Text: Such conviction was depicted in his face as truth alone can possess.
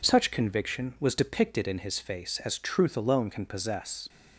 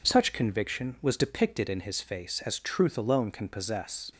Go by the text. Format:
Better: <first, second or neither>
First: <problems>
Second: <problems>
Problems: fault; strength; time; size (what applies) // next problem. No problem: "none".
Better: neither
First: none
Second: none